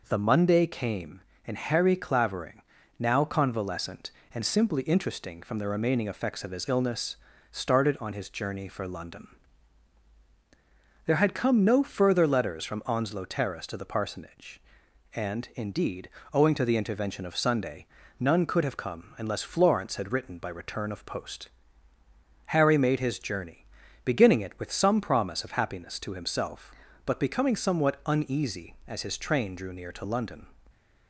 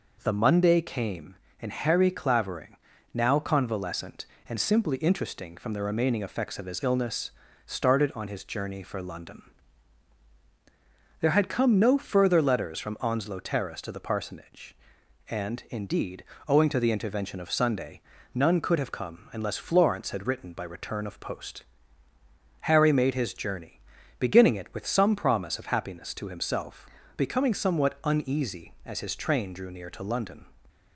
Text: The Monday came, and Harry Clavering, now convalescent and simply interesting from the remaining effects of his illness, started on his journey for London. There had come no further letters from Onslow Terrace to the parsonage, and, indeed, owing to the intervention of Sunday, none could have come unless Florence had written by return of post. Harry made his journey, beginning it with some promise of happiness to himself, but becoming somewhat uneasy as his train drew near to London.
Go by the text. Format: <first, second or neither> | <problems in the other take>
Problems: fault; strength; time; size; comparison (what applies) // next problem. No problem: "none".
first | skips "but"; at 27.0 s